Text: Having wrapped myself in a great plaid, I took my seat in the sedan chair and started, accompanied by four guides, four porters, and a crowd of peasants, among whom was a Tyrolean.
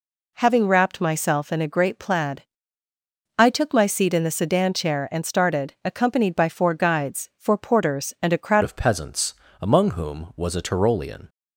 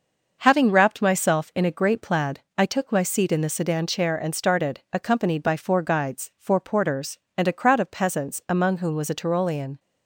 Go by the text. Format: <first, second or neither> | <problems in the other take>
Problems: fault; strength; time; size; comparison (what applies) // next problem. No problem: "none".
second | changes voice at "of"; from 8.6 s on; 2.6 s long